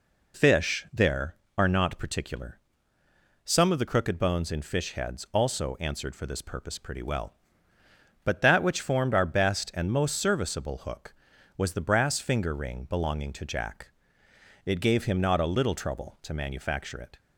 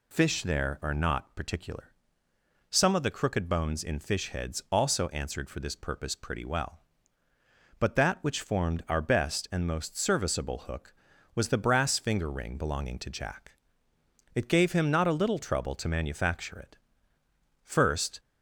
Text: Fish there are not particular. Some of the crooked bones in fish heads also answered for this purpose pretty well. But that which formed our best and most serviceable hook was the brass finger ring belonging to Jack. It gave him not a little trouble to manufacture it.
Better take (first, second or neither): first